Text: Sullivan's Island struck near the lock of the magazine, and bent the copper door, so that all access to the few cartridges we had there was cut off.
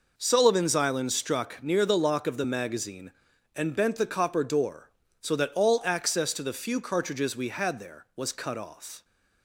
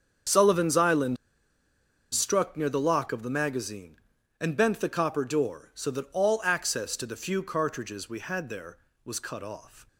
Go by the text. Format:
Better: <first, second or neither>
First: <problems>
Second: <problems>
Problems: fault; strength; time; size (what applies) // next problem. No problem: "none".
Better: first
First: none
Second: starts louder than the rest; strong; until 2.2 s; 7.5 dB // pauses between "Island" and "struck"; noticeable; at 1.1 s; 0.96 s long